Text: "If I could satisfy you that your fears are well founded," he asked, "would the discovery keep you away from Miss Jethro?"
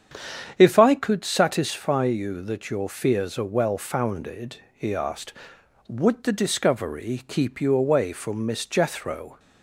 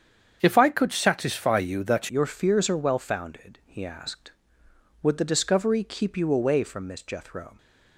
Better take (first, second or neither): first